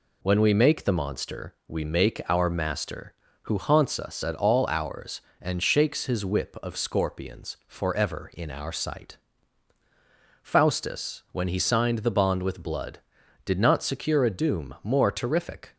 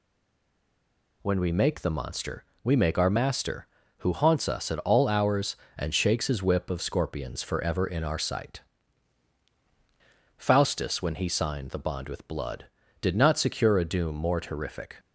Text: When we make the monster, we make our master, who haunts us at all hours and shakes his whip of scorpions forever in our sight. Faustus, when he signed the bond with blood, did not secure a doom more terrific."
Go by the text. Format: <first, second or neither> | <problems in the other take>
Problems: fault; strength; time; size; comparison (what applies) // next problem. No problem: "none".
first | stays silent before the first word; noticeable; until 1.2 s; 1.2 s long